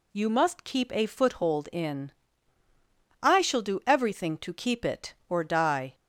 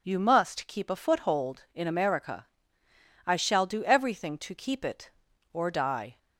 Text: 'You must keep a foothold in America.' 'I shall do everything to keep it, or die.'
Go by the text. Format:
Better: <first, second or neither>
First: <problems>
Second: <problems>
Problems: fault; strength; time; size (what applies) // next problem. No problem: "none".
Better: second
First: skips "America"; at 2.6 s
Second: none